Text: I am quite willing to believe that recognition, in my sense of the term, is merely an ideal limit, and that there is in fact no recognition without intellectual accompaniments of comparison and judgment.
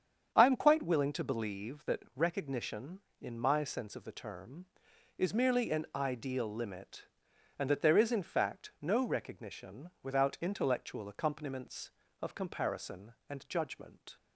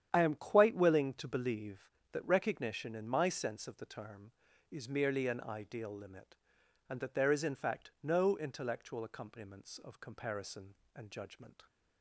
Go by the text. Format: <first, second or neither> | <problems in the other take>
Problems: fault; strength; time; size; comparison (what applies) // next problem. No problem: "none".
first | starts louder than the rest; strong; until 1.1 s; 9.5 dB; strong in the first // skips "recognition without"; at 8.3 s